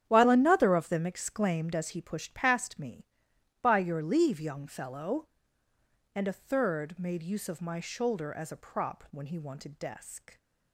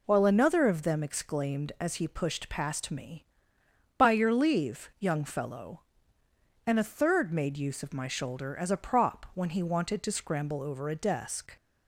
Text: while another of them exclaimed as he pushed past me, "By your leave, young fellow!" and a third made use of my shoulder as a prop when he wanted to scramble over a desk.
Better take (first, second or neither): second